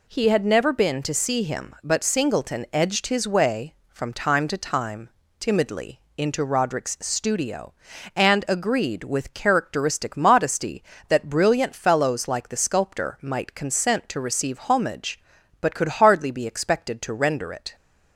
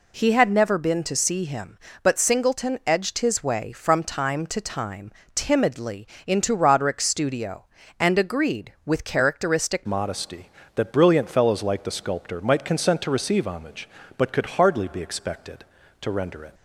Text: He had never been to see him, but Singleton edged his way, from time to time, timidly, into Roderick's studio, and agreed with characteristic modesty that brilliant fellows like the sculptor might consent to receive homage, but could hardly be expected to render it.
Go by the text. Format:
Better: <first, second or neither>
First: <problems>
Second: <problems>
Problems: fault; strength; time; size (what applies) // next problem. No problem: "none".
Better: first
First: none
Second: changes voice at "modesty"; from 9.8 s on; 6.7 s long